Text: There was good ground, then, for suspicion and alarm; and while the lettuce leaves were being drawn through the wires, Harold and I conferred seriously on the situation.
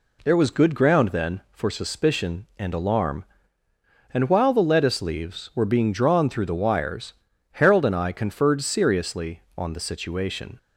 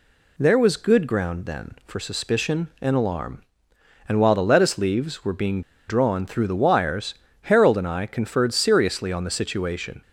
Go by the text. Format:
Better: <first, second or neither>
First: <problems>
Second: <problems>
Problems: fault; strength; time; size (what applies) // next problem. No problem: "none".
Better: first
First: none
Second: pauses between "being" and "drawn"; slight; at 5.6 s; 0.27 s long